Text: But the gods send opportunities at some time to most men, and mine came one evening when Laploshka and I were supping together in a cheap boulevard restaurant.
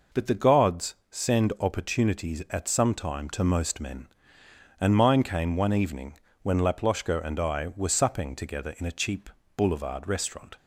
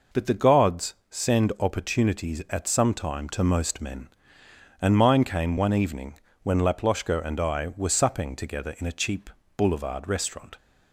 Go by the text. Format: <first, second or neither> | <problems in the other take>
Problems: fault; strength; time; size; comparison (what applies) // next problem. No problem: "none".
neither | pauses between "evening" and "when"; slight; the same in both // pauses between "cheap" and "boulevard"; slight; the same in both